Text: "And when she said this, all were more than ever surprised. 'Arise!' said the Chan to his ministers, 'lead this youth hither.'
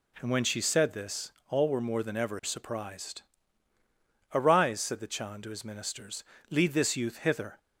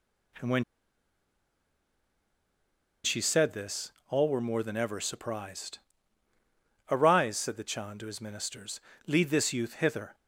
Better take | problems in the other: first | pauses between "when" and "she"; strong; at 0.6 s; 2.4 s long

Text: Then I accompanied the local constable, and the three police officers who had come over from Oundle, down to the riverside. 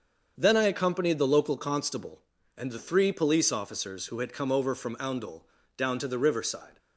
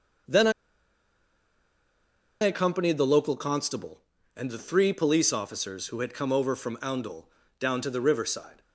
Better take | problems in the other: first | starts louder than the rest; until 3.1 s; 7 dB; also in the first // pauses between "I" and "accompanied"; strong; at 0.5 s; 1.9 s long

